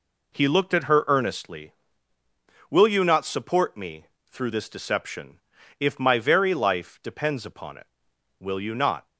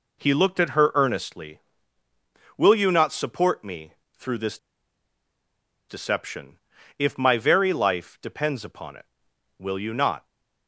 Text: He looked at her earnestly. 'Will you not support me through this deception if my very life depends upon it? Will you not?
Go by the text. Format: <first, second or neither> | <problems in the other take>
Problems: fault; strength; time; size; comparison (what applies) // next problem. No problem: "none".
first | pauses between "me" and "through"; slight; at 3.9 s; 0.24 s long; slight in the first // pauses between "this" and "deception"; strong; at 4.5 s; 1.3 s long // pauses between "deception" and "if"; at 6.5 s; 0.40 s long; also in the first